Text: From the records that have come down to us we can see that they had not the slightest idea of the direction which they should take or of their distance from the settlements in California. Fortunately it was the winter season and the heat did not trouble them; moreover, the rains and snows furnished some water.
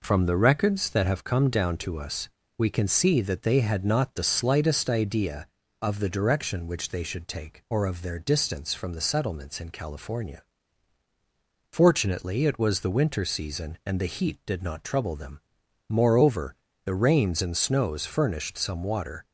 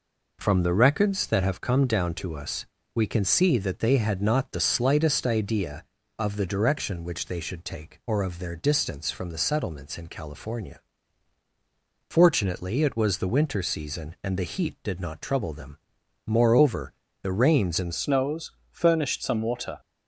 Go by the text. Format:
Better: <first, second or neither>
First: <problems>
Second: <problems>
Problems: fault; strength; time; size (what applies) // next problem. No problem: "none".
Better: first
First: pauses between "us" and "we"; slight; at 2.2 s; 0.30 s long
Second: pauses between "us" and "we"; slight; at 2.6 s; 0.30 s long // changes voice at "snows"; from 17.9 s on; 1.8 s long // pauses between "snows" and "furnished"; slight; at 18.5 s; 0.20 s long